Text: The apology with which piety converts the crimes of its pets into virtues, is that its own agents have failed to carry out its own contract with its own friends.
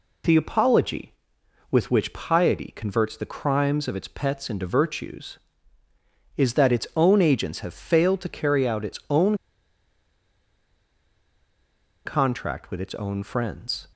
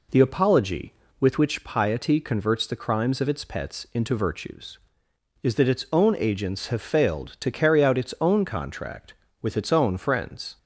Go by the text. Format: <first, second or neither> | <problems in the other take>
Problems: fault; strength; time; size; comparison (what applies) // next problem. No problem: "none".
second | pauses between "own" and "contract"; strong; at 9.3 s; 2.6 s long